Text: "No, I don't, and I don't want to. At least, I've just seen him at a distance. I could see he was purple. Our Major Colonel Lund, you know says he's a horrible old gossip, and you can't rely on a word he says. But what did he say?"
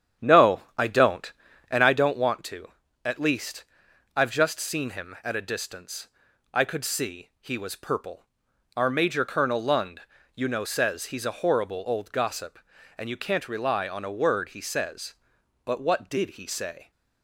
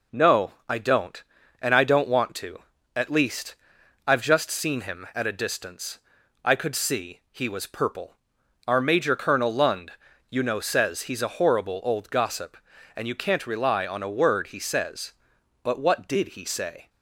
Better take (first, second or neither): second